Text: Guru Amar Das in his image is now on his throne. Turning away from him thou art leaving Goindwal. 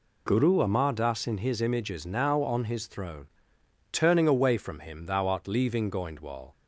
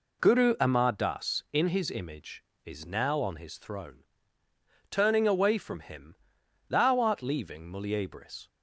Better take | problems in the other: first | pauses between "him" and "thou"; noticeable; at 6.1 s; 0.54 s long // says "Muliebris" for "Goindwal"; at 7.7 s

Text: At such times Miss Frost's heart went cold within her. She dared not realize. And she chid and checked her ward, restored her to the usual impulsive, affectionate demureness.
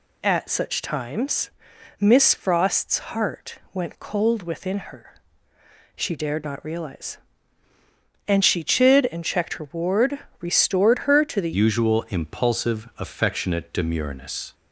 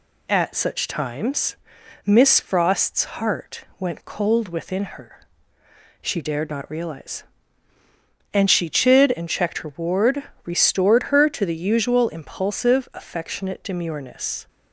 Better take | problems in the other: second | pauses between "times" and "Miss"; noticeable; at 1.4 s; 0.50 s long; noticeable in the second // pauses between "Frost's" and "heart"; slight; at 2.9 s; 0.16 s long; slight in the second // pauses between "heart" and "went"; slight; at 3.5 s; 0.16 s long; slight in the second // changes voice at "usual"; from 11.5 s on; 3.0 s long

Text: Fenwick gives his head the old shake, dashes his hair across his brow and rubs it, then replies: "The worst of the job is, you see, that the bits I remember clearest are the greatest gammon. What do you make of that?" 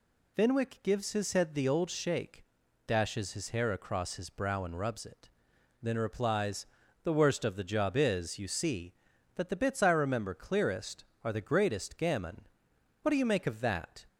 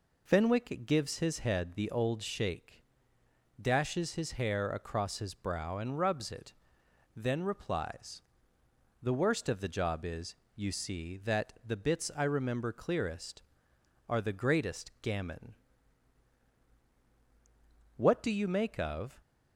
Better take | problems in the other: first | stops before "that"; at 19.2 s

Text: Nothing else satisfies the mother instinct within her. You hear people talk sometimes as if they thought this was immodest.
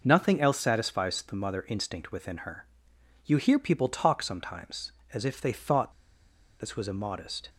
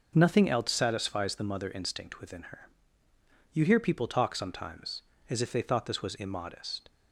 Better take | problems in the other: second | pauses between "thought" and "this"; noticeable; at 5.9 s; 0.68 s long

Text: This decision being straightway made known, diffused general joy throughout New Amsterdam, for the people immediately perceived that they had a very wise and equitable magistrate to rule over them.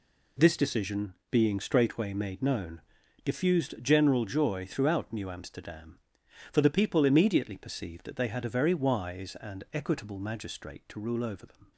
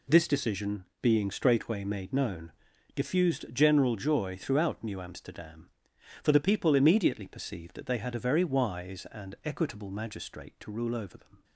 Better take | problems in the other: neither | pauses between "decision" and "being"; slight; the same in both

